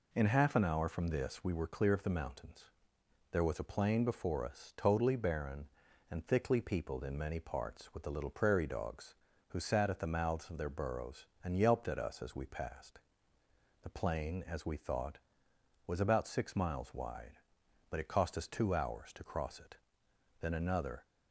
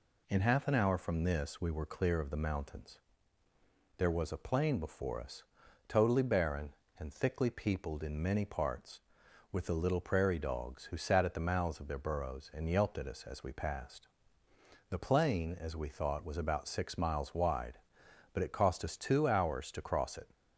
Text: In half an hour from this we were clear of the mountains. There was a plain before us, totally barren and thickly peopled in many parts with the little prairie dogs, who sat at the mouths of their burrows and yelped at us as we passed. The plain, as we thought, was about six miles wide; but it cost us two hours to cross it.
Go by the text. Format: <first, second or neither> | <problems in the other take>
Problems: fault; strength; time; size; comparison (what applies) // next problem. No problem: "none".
second | goes on to say "Then another"; noticeable; from 20.4 s on; 0.64 s long